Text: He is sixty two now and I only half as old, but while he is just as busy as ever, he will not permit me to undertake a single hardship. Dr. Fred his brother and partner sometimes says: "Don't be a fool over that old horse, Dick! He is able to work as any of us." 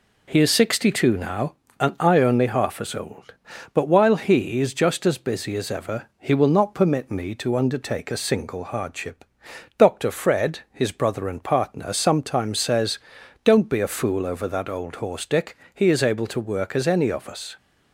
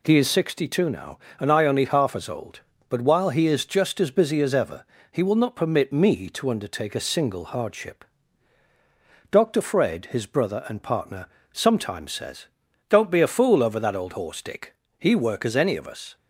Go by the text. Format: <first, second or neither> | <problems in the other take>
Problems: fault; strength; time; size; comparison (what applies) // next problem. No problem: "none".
first | pauses between "partner" and "sometimes"; slight; at 11.2 s; 0.26 s long // skips "is able to"; at 15.1 s